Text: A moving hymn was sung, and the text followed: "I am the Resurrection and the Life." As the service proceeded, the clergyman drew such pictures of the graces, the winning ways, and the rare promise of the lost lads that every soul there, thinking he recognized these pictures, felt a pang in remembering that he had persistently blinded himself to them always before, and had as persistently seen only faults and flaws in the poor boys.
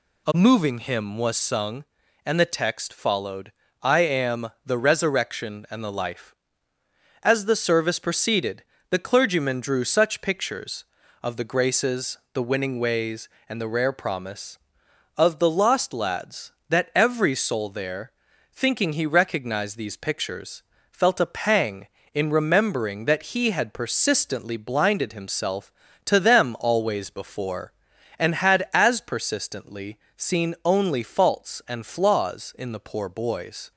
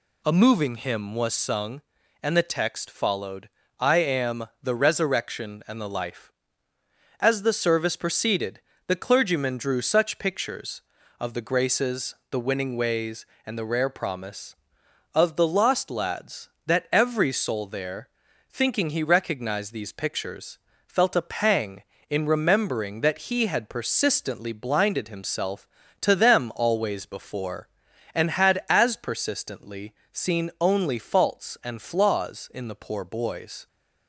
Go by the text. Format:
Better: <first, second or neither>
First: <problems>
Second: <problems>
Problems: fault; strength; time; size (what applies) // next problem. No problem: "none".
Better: neither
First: pauses between "am" and "the"; slight; at 4.4 s; 0.16 s long // pauses between "persistently" and "seen"; slight; at 29.9 s; 0.20 s long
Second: pauses between "am" and "the"; slight; at 4.4 s; 0.16 s long // pauses between "persistently" and "seen"; slight; at 29.9 s; 0.20 s long